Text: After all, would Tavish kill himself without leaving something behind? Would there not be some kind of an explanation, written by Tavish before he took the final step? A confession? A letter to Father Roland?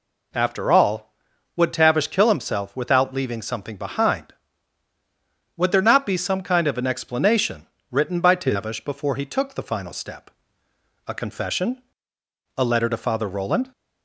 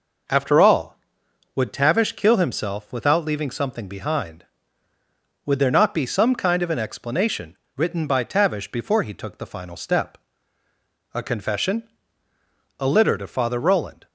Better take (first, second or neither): first